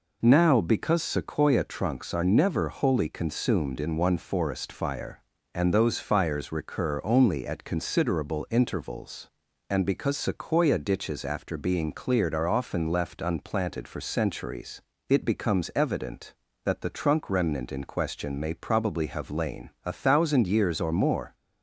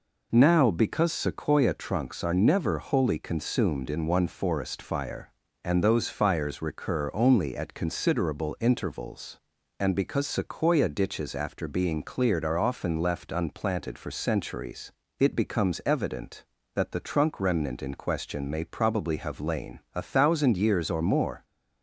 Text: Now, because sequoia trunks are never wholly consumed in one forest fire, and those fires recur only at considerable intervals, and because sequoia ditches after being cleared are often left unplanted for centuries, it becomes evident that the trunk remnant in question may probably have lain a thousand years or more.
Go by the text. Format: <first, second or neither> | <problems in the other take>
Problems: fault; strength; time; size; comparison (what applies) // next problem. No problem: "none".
neither | pauses between "lain" and "a"; slight; the same in both